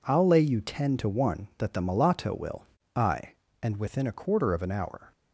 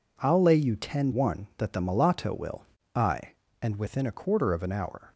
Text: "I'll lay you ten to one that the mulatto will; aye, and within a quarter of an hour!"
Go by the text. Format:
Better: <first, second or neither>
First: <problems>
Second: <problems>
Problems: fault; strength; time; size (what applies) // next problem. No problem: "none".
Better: first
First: none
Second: skips "to"; at 1.1 s